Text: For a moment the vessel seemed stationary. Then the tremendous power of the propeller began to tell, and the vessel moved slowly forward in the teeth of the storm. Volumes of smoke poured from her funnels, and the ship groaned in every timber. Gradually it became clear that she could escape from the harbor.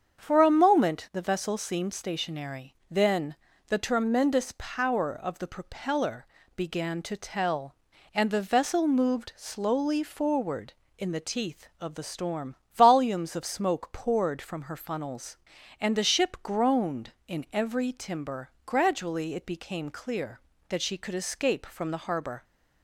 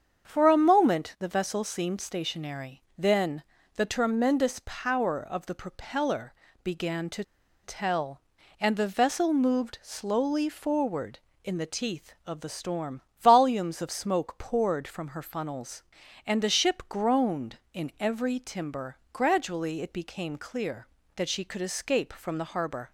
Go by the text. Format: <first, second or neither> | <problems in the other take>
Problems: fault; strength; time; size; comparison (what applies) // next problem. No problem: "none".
first | starts louder than the rest; strong; until 1.3 s; 7 dB; strong in the first // pauses between "Then" and "the"; slight; at 3.4 s; 0.32 s long; slight in the first // pauses between "propeller" and "began"; slight; at 6.3 s; 0.30 s long; slight in the first // pauses between "to" and "tell"; at 7.2 s; 0.41 s long